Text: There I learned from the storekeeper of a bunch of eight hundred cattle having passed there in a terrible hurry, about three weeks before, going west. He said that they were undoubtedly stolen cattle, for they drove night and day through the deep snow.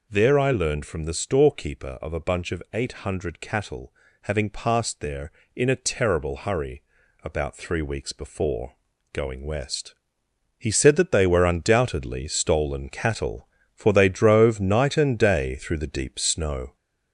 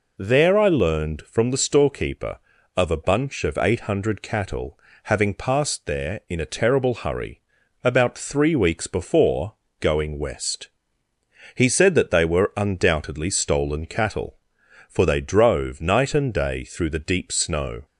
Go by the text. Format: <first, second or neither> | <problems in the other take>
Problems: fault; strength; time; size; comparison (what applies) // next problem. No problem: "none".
second | gets louder; slight; throughout; 3 dB // pauses between "cattle" and "having"; slight; at 3.9 s; 0.30 s long; slight in the second